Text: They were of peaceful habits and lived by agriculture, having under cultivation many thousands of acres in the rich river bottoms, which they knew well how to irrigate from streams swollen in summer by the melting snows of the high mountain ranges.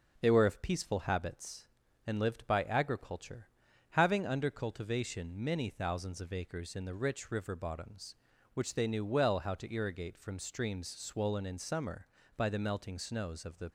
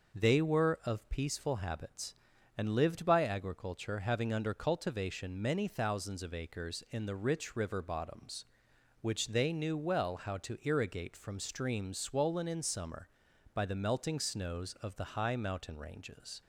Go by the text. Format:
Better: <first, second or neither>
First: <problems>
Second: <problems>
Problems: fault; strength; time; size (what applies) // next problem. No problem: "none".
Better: second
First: stops before "high mountain ranges"; at 13.6 s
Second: none